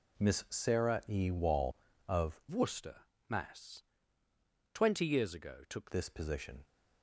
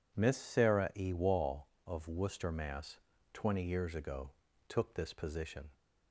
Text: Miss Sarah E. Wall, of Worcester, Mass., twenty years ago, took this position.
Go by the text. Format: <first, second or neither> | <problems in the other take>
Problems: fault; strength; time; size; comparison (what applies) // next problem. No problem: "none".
second | changes voice from "Worcester" to "took"; from 2.5 to 5.9 s; 3.4 s long